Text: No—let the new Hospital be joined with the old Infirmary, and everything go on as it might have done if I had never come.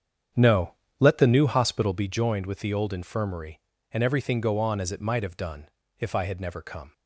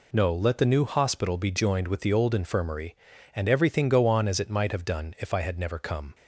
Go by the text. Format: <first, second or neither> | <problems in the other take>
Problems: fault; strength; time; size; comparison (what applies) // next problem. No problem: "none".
second | starts louder than the rest; strong; until 2.2 s; 8 dB // pauses between "done" and "if"; slight; at 5.6 s; 0.30 s long